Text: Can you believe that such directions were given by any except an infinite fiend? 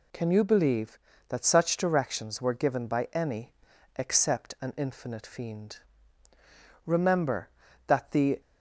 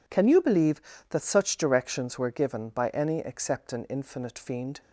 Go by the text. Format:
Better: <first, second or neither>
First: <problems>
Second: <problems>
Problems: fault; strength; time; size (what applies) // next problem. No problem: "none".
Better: second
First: pauses between "any" and "except"; at 3.5 s; 0.44 s long // goes on to say "Remember that the"; from 6.8 s on; 1.5 s long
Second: none